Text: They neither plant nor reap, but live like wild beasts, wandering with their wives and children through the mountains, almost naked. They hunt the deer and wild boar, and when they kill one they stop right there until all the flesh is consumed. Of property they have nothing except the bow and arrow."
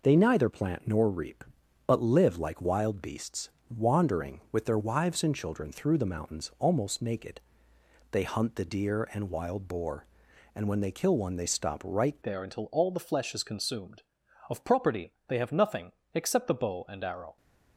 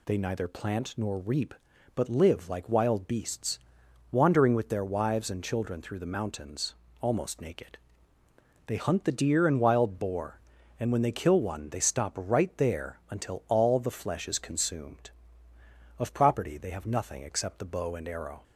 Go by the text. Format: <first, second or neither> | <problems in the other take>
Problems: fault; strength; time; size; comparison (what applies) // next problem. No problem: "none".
second | changes voice at "there"; from 12.2 s on; 5.1 s long // pauses between "nothing" and "except"; slight; at 15.9 s; 0.20 s long